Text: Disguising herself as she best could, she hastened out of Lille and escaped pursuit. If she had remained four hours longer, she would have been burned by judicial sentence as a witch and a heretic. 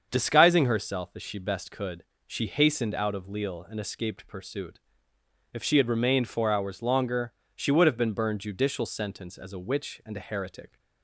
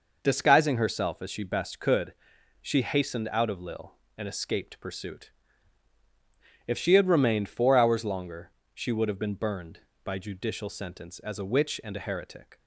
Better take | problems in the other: second | starts louder than the rest; until 1.1 s; 7 dB // skips "by"; at 8.4 s

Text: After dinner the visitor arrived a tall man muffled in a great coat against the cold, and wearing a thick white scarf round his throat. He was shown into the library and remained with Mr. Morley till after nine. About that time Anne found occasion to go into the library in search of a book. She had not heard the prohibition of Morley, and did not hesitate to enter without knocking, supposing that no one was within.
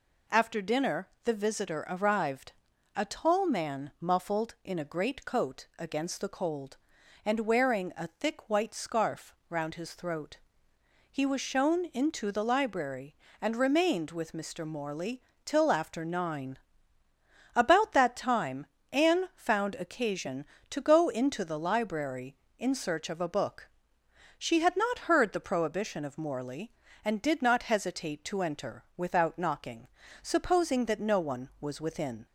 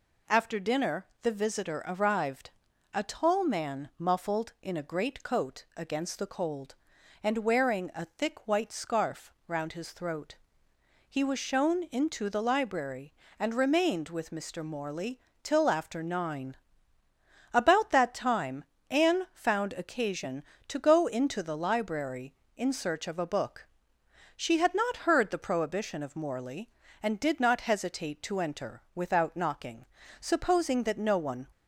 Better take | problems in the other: first | pauses between "dinner" and "the"; slight; at 1.0 s; 0.16 s long; slight in the first // pauses between "arrived" and "a"; at 2.4 s; 0.44 s long; also in the first // pauses between "Morley" and "till"; slight; at 15.1 s; 0.24 s long; slight in the first // pauses between "time" and "Anne"; slight; at 18.6 s; 0.26 s long; slight in the first // stops before "was within"; at 31.5 s

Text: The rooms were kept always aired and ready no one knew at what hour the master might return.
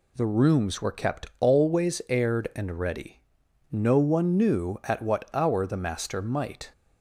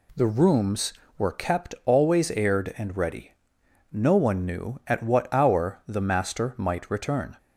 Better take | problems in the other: second | pauses between "ready" and "no"; noticeable; at 3.1 s; 0.52 s long; noticeable in the second // stops before "return"; at 6.7 s

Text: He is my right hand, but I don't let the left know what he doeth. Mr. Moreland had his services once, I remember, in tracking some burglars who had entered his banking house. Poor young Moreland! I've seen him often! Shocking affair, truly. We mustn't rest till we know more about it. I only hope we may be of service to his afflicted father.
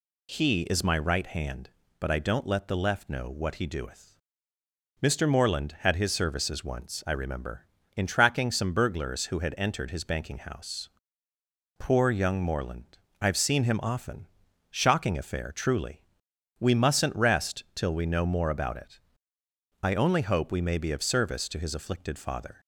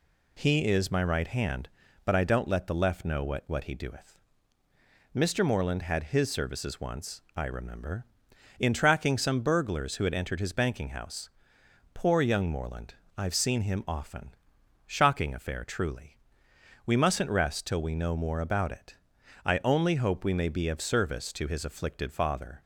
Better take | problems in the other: first | says "what" twice; at 3.4 s

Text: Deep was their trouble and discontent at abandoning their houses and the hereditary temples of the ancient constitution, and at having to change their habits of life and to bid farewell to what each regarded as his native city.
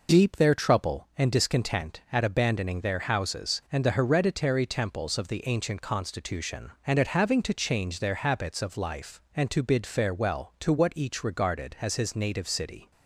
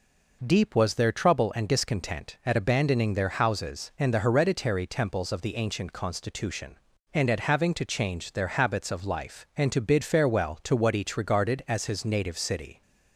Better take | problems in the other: second | skips "was"; at 0.3 s

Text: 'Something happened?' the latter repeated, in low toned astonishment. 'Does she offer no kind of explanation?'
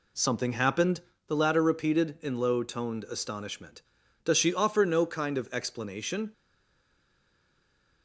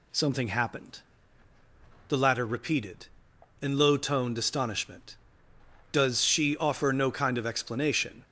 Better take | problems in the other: second | stays silent after the last word; noticeable; from 6.3 s on; 1.7 s long

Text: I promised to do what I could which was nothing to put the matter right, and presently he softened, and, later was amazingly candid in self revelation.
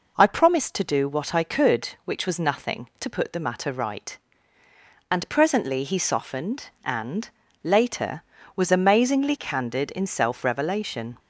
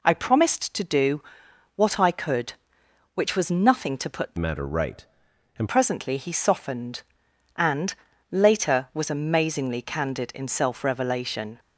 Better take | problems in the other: first | pauses between "do" and "what"; noticeable; at 1.2 s; 0.56 s long // changes voice from "matter" to "and"; from 4.3 to 5.6 s; 1.3 s long

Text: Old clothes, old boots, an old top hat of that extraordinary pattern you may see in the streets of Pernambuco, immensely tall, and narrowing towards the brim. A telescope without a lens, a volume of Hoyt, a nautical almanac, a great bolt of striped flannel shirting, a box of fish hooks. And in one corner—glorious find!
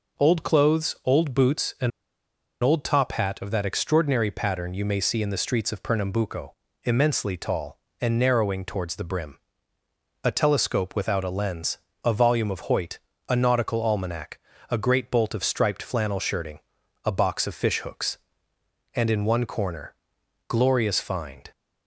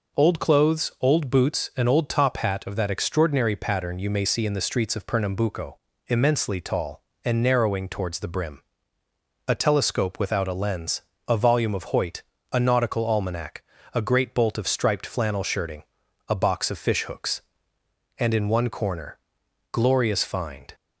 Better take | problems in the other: second | pauses between "an" and "old"; noticeable; at 1.9 s; 0.72 s long

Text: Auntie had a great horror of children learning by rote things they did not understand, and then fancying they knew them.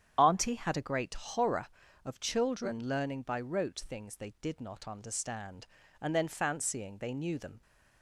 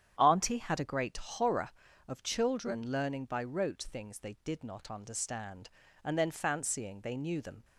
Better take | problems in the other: second | loses the start of "Auntie"; at 0.1 s; 30 ms // starts louder than the rest; strong; until 1.1 s; 9 dB; strong in the second

